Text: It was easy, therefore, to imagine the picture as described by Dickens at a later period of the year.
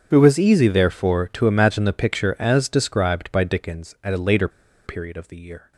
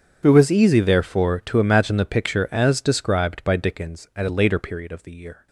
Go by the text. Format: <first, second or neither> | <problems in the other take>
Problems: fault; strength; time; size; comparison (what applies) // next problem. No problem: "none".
second | starts louder than the rest; strong; until 1.1 s; 8 dB; strong in the second // pauses between "later" and "period"; at 4.4 s; 0.36 s long